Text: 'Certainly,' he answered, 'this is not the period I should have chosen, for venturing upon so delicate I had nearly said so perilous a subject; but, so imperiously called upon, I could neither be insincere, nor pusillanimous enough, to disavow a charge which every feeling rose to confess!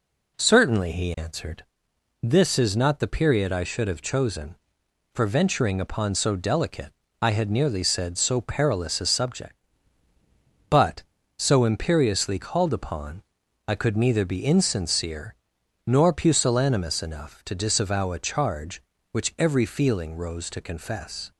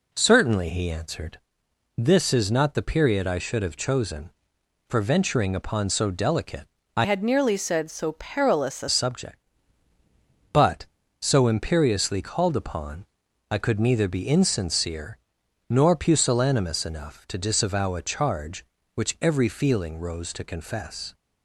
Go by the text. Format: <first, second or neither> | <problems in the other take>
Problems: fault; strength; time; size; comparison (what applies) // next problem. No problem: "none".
first | pauses between "delicate" and "I"; slight; at 6.6 s; 0.28 s long; slight in the first // changes voice from "had" to "a"; from 7.0 to 8.8 s; 1.8 s long